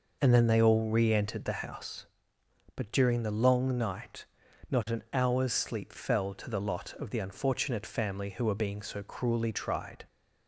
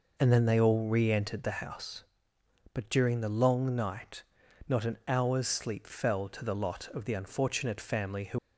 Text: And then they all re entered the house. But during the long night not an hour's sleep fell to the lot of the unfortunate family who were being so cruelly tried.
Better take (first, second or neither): first